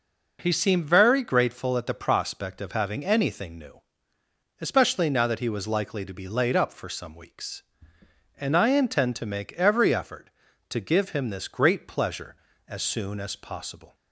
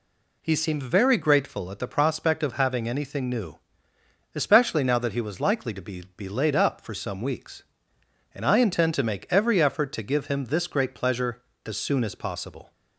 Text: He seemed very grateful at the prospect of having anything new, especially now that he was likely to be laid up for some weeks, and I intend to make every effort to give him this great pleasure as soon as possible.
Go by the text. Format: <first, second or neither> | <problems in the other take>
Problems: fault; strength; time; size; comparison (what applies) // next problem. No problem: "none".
first | says "be" twice; at 6.1 s